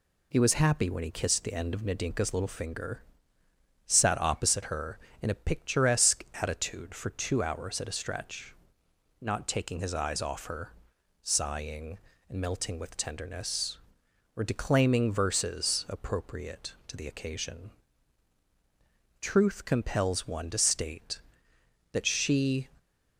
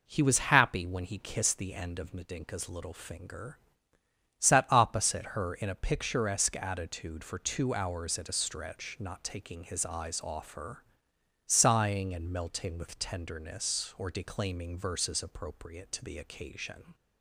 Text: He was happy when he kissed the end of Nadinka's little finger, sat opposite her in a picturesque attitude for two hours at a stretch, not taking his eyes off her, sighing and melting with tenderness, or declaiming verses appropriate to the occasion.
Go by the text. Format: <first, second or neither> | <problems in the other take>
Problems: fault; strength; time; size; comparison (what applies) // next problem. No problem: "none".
second | pauses between "picturesque" and "attitude"; slight; at 6.2 s; 0.16 s long // goes on to say "Truth compels one to state that she"; strong; from 19.1 s on; 3.4 s long